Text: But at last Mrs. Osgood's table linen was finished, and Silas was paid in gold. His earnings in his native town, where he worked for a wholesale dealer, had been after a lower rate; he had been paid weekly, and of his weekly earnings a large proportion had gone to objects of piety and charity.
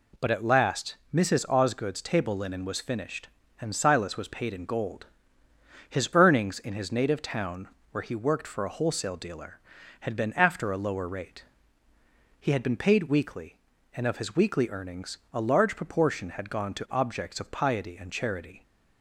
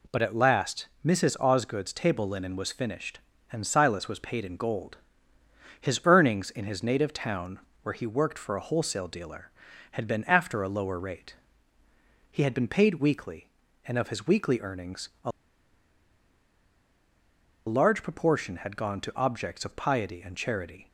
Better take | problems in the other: first | pauses between "a" and "large"; strong; at 15.3 s; 2.3 s long

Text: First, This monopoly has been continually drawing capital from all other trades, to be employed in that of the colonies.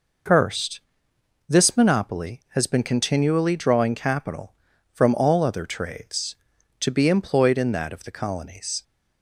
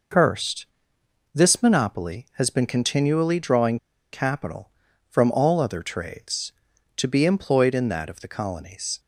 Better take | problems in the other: first | pauses between "drawing" and "capital"; slight; at 3.7 s; 0.34 s long

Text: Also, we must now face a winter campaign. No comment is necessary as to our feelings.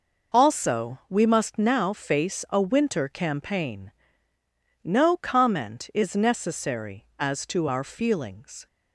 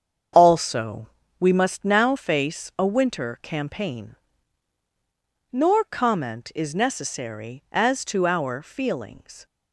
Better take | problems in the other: first | starts louder than the rest; strong; until 1.6 s; 7.5 dB // says "Nor" for "No"; at 5.5 s

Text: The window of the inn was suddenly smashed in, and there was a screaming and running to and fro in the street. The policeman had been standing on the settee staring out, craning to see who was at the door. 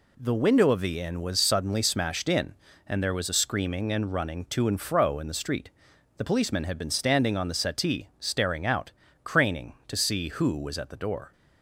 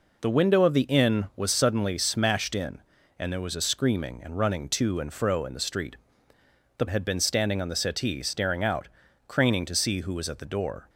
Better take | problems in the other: first | skips "policeman"; at 6.8 s

